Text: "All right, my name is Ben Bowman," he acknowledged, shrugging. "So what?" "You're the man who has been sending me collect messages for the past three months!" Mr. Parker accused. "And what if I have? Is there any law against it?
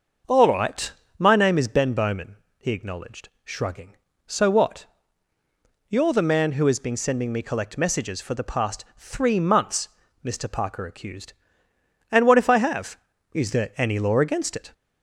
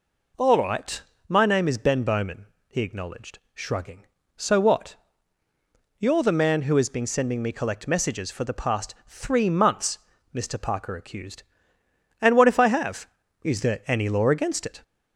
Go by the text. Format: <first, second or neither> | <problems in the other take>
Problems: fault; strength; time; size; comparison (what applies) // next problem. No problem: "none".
second | starts louder than the rest; until 1.9 s; 6.5 dB